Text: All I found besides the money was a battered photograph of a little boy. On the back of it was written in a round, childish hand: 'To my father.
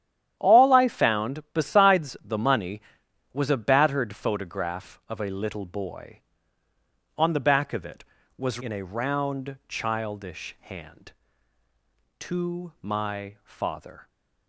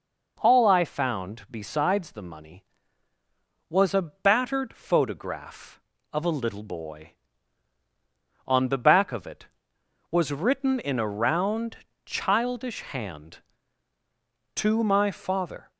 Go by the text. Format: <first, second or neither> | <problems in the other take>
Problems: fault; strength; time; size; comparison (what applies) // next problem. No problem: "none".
second | starts louder than the rest; strong; until 1.4 s; 10.5 dB // skips "written"; at 8.5 s